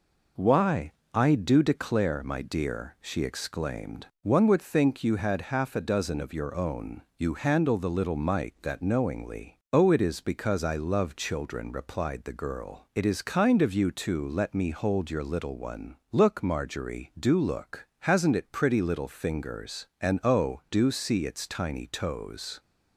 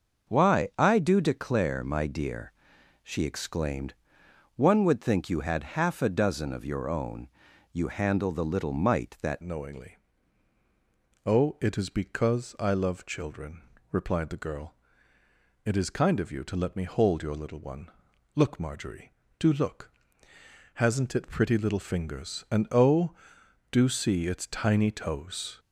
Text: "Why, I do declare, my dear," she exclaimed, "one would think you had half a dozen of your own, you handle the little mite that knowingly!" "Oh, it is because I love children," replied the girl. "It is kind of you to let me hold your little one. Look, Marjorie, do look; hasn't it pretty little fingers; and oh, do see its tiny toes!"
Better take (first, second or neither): first